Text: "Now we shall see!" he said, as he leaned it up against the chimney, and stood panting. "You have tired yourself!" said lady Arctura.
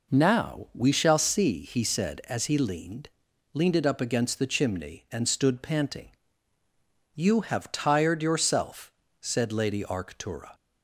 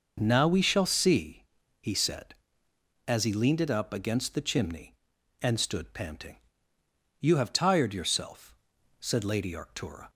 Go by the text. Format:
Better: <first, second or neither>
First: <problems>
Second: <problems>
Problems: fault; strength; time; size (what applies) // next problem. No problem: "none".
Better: second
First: says "leaned" twice; at 3.5 s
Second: none